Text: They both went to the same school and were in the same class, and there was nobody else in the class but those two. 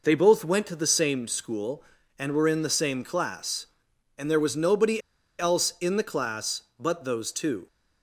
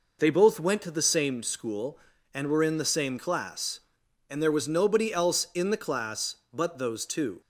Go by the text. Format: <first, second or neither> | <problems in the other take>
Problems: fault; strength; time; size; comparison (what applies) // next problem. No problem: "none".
second | pauses between "nobody" and "else"; at 5.0 s; 0.38 s long